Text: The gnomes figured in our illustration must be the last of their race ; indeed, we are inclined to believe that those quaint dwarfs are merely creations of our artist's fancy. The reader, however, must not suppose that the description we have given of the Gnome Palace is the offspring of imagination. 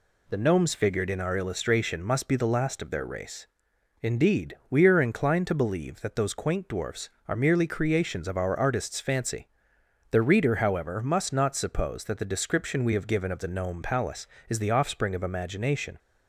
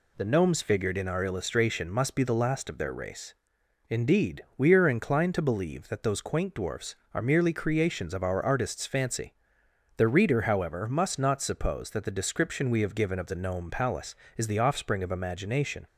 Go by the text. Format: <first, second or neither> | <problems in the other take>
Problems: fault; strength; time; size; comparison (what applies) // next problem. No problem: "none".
neither | none